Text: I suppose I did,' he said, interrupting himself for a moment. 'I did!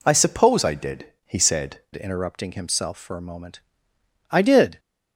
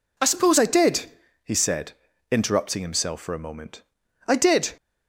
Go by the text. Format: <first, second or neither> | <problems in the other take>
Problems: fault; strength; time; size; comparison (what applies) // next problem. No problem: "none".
second | changes voice at "interrupting"; from 1.9 s on; 2.8 s long